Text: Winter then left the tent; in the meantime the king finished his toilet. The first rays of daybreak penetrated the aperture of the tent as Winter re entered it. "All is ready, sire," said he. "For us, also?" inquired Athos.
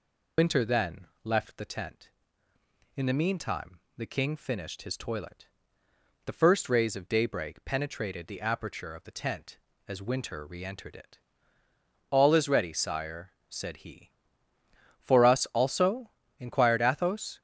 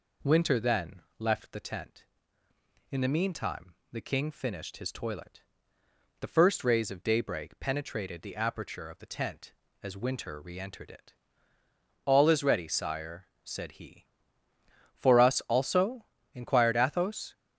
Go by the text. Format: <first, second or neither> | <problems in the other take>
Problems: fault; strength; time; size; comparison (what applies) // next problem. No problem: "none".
second | loses the start of "Winter"; at 0.3 s; 125 ms // pauses between "then" and "left"; slight; at 1.0 s; 0.16 s long; slight in the second // pauses between "meantime" and "the"; slight; at 3.7 s; 0.18 s long; slight in the second